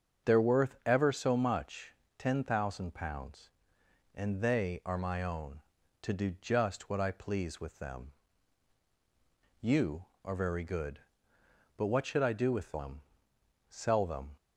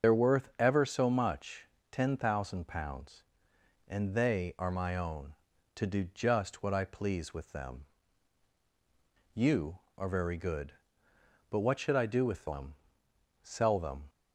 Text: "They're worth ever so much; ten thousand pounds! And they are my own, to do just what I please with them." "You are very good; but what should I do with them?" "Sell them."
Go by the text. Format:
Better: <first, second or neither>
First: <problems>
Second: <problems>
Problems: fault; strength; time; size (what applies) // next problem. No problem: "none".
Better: first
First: starts louder than the rest; until 1.3 s; 6.5 dB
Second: loses the start of "They're"; at 0.0 s; 45 ms // starts louder than the rest; until 1.1 s; 6.5 dB